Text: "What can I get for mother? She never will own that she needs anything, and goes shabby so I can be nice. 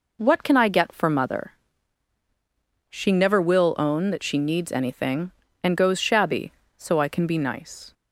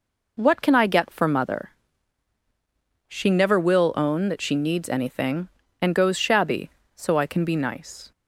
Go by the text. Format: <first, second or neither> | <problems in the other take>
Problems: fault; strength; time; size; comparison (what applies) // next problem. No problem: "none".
neither | none